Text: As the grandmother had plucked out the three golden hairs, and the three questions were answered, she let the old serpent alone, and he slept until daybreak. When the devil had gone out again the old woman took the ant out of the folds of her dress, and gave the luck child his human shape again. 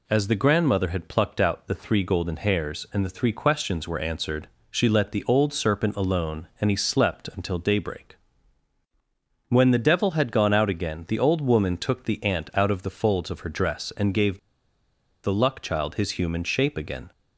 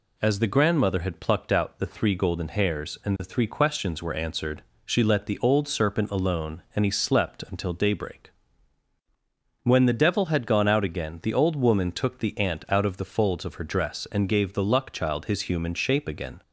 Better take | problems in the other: second | pauses between "gave" and "the"; noticeable; at 14.3 s; 0.86 s long

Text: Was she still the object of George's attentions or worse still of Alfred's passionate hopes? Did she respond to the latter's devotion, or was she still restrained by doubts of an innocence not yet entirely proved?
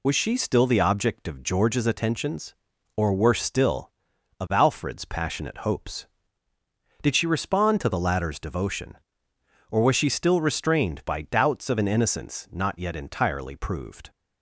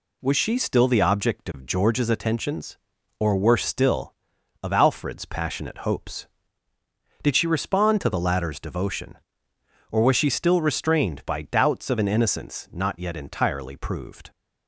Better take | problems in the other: second | loses the start of "Was"; at 0.0 s; 40 ms

